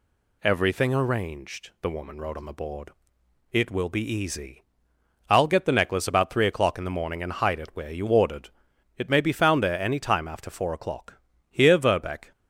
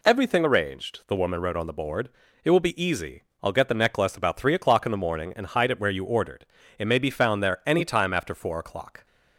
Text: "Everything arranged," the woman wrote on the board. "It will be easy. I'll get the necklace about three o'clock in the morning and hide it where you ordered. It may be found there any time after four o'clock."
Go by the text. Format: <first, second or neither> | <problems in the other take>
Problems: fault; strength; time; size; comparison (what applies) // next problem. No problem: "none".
second | goes on to say "Here Verbeck"; noticeable; from 11.4 s on; 0.82 s long